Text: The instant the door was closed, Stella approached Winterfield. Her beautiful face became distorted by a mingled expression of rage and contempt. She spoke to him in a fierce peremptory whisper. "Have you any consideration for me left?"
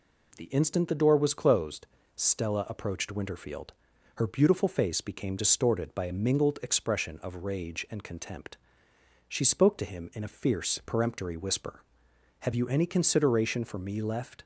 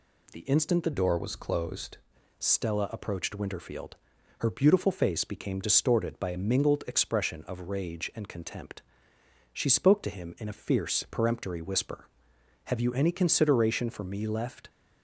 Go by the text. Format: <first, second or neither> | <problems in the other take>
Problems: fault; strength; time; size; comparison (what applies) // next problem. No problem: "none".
first | changes voice from "door" to "closed"; from 0.9 to 1.9 s; 1.0 s long